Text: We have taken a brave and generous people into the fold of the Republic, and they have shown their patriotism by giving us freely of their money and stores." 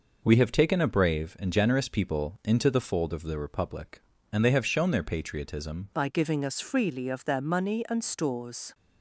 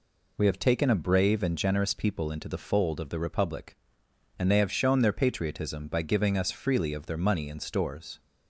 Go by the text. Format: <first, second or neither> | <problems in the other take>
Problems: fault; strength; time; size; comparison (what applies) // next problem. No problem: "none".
second | changes voice at "by"; from 5.9 s on; 2.8 s long